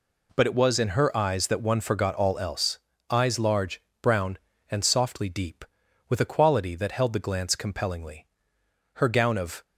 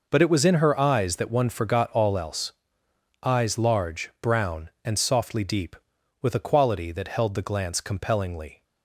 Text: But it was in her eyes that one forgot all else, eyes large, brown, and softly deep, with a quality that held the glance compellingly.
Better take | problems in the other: second | goes on to say "Her gown of"; noticeable; from 8.9 s on; 0.68 s long

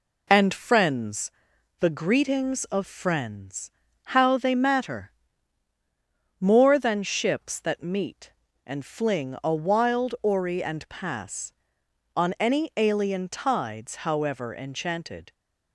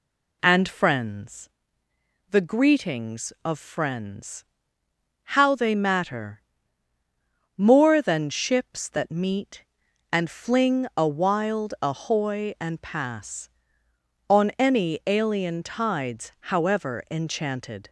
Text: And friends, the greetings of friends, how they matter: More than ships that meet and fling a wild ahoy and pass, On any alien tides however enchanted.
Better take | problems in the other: second | says "ori" for "ahoy"; at 10.2 s

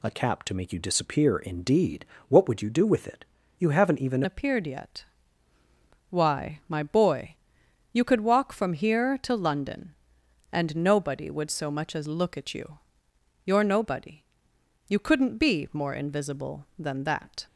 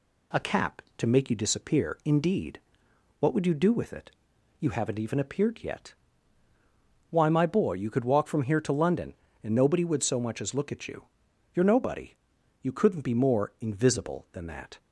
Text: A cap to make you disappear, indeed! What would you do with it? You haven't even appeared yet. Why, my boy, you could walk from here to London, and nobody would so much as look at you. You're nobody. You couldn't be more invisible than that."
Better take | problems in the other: second | changes voice at "appeared"; from 4.2 s on; 13.2 s long

